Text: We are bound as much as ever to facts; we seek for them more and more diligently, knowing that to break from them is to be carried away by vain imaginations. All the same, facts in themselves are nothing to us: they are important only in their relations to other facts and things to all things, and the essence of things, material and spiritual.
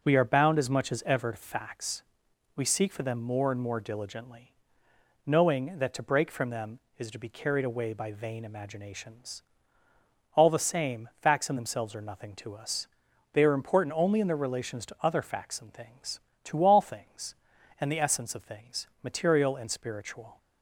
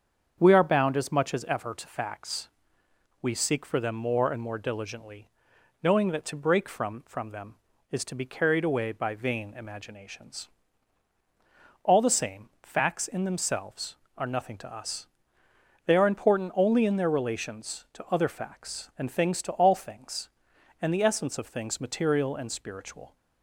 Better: first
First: starts louder than the rest; until 1.0 s; 6.5 dB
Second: starts louder than the rest; strong; until 1.4 s; 7.5 dB // says "from" twice; at 7.0 s

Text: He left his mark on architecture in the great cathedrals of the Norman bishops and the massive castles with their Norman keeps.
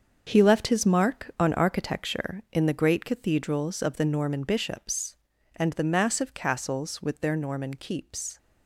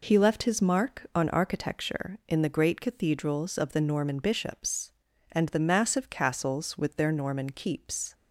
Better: second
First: gets quieter; strong; throughout; 9.5 dB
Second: none

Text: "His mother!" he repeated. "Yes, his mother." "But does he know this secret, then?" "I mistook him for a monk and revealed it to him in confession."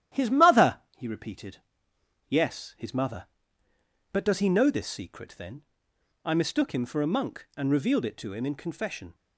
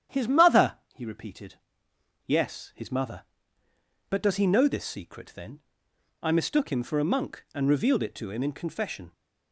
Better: second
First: gets quieter; throughout; 3.5 dB // starts louder than the rest; strong; until 1.2 s; 11.5 dB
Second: starts louder than the rest; strong; until 1.2 s; 9.5 dB

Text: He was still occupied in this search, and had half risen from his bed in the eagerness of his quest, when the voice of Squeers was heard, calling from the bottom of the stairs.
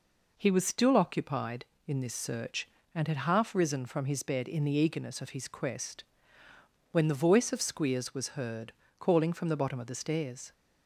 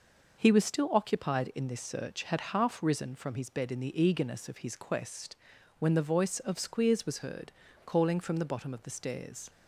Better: first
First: none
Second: skips "and"; at 2.2 s

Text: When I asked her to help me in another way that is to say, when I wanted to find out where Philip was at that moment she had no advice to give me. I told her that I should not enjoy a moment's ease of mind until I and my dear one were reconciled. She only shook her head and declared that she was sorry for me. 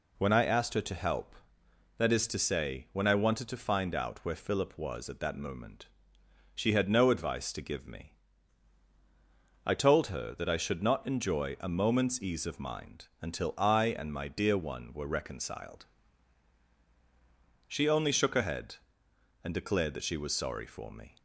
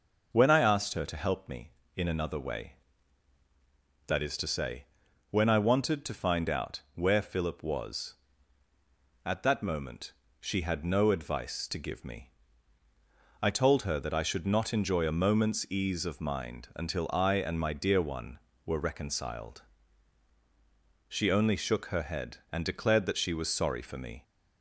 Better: second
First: skips "me in another way"; at 1.6 s // pauses between "moment" and "she"; noticeable; at 5.8 s; 0.68 s long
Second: pauses between "moment" and "she"; slight; at 10.1 s; 0.26 s long

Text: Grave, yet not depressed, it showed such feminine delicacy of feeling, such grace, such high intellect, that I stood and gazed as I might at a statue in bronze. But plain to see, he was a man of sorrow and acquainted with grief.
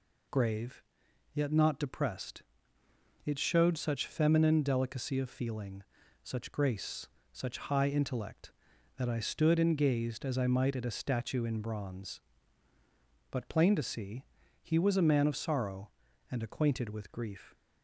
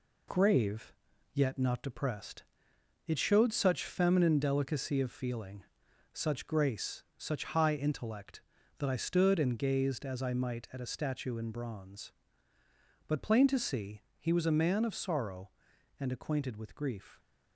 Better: first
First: none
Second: gets quieter; noticeable; throughout; 5 dB

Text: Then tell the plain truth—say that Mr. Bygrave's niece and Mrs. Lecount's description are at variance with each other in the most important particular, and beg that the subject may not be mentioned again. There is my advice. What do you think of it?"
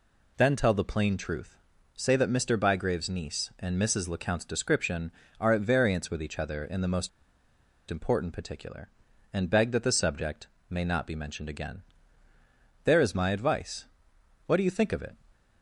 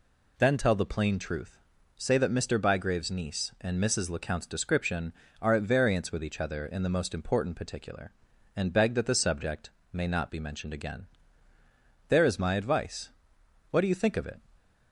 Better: second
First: pauses between "most" and "important"; noticeable; at 7.0 s; 0.81 s long // pauses between "subject" and "may"; slight; at 10.4 s; 0.22 s long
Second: pauses between "subject" and "may"; slight; at 9.6 s; 0.22 s long

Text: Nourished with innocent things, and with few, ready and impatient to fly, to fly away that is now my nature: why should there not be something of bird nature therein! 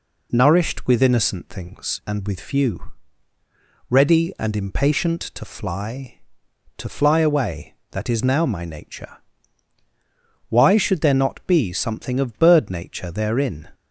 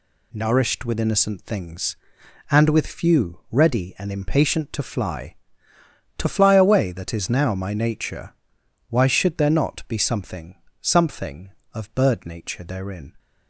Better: first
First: none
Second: says "something" twice; at 10.8 s

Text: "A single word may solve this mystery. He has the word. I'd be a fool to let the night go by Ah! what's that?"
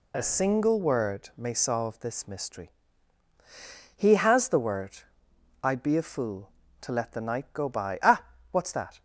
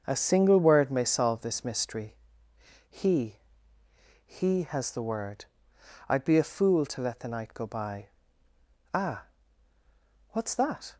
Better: first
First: none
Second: starts louder than the rest; until 1.0 s; 6.5 dB // says "He" twice; at 4.2 s // pauses between "by" and "Ah"; noticeable; at 8.0 s; 0.84 s long

